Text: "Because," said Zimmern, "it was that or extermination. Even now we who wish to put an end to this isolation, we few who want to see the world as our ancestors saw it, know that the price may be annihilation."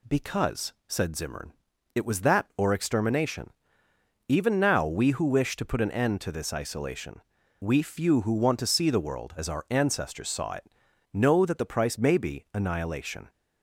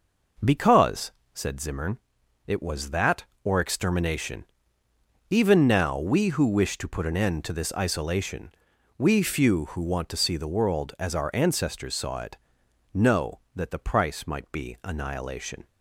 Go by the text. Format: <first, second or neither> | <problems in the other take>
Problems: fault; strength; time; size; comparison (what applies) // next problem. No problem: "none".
first | says "might" for "may"; at 14.2 s